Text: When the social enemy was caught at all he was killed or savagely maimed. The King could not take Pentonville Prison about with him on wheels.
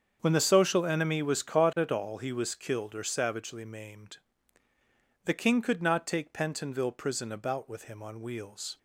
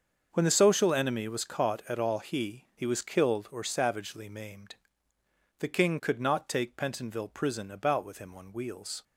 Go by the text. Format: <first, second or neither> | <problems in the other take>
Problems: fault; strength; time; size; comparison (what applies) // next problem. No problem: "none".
first | starts louder than the rest; until 1.3 s; 6.5 dB; strong in the first // says "he" twice; at 2.7 s